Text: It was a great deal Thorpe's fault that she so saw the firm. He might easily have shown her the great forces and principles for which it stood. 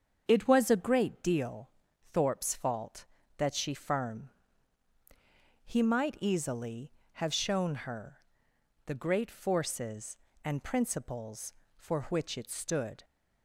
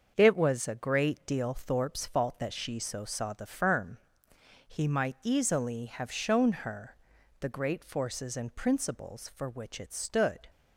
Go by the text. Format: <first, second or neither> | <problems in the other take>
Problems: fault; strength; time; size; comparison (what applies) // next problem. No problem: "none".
second | starts louder than the rest; strong; until 1.2 s; 7.5 dB; also in the second // pauses between "deal" and "Thorpe's"; at 1.7 s; 0.42 s long // skips "so saw the"; at 3.7 s // pauses between "her" and "the"; noticeable; at 8.1 s; 0.70 s long; also in the second